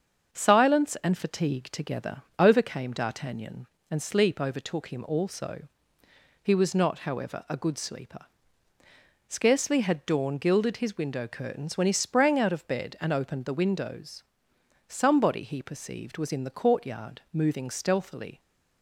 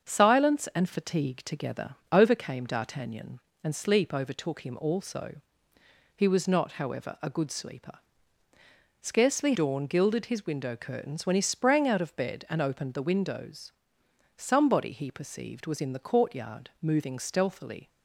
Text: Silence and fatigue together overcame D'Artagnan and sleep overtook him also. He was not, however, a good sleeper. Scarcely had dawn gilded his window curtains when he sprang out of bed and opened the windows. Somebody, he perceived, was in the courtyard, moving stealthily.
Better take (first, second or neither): first